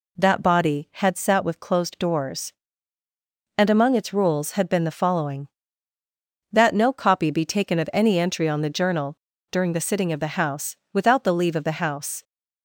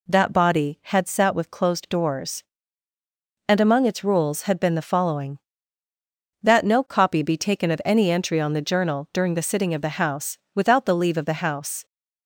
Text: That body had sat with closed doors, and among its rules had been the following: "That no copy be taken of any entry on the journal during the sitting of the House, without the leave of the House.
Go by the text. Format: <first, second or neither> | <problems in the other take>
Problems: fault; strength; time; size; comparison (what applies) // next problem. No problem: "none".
second | pauses between "journal" and "during"; slight; at 9.1 s; 0.32 s long